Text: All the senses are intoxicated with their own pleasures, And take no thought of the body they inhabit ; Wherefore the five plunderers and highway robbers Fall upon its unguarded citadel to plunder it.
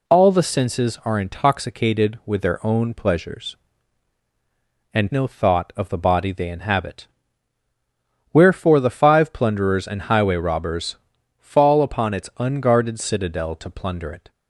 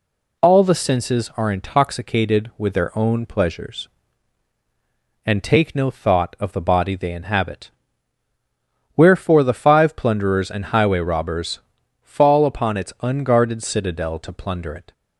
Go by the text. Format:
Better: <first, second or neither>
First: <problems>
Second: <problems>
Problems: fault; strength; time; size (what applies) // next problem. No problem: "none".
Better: second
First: skips "take"; at 5.0 s // pauses between "robbers" and "Fall"; at 10.9 s; 0.44 s long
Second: pauses between "robbers" and "Fall"; at 11.5 s; 0.44 s long